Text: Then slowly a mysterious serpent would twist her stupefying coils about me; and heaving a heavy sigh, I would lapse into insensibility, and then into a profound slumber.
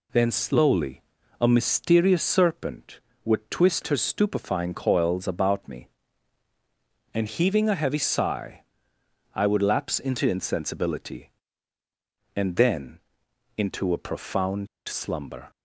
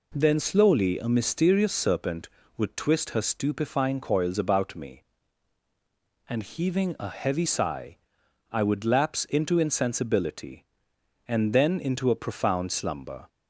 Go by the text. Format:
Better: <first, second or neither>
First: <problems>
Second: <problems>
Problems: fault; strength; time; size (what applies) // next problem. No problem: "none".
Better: second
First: pauses between "slowly" and "a"; at 1.0 s; 0.38 s long // pauses between "then" and "into"; noticeable; at 12.9 s; 0.58 s long // pauses between "profound" and "slumber"; slight; at 14.6 s; 0.18 s long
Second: none